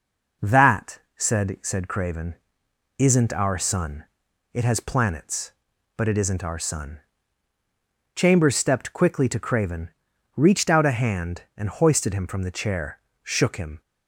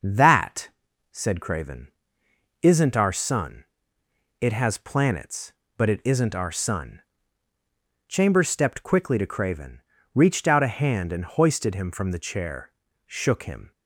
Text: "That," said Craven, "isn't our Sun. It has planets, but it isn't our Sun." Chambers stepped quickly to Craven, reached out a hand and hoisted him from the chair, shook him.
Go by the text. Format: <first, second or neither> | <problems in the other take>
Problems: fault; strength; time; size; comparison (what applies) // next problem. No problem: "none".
second | says "said" twice; at 1.6 s